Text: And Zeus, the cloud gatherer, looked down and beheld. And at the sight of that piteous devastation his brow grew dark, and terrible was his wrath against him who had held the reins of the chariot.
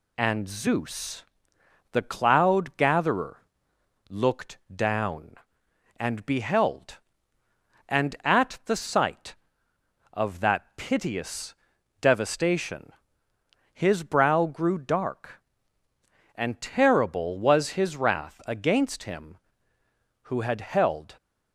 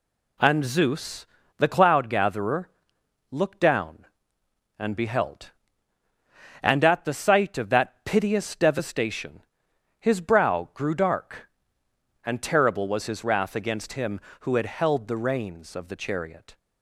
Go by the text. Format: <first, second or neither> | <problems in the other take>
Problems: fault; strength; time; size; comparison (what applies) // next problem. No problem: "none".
second | pauses between "looked" and "down"; slight; at 4.5 s; 0.16 s long // pauses between "piteous" and "devastation"; noticeable; at 11.5 s; 0.46 s long // pauses between "devastation" and "his"; noticeable; at 12.9 s; 0.82 s long; noticeable in the second // stops before "the reins of the chariot"; at 21.1 s